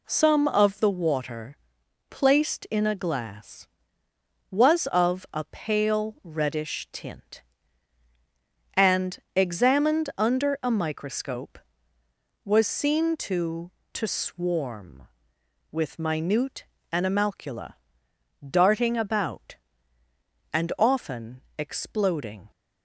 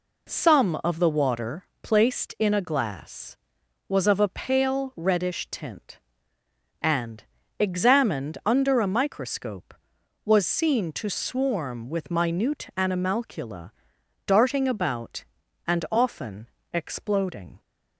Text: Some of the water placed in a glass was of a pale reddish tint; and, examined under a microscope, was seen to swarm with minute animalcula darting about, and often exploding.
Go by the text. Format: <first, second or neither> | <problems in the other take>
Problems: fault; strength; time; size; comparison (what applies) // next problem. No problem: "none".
second | pauses between "water" and "placed"; noticeable; at 1.5 s; 0.54 s long; slight in the second // says "to" twice; at 13.9 s // pauses between "minute" and "animalcula"; slight; at 16.6 s; 0.26 s long // pauses between "animalcula" and "darting"; noticeable; at 17.7 s; 0.74 s long; noticeable in the second // pauses between "often" and "exploding"; slight; at 21.4 s; 0.16 s long; slight in the second